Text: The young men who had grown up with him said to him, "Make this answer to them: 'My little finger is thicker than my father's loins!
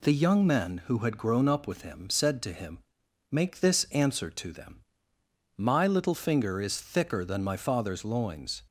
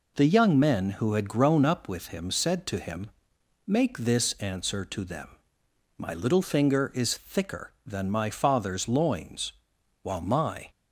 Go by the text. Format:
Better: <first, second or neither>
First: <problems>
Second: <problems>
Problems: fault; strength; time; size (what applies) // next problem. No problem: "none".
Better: first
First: none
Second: goes on to say "While my"; noticeable; from 10.0 s on; 0.68 s long